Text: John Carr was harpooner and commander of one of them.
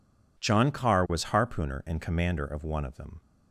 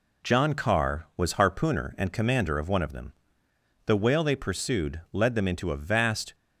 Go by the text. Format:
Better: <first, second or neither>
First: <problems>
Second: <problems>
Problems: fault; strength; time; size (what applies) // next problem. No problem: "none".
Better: first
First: none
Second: goes on to say "The whale they pursued led them into a vast"; strong; from 3.8 s on; 2.4 s long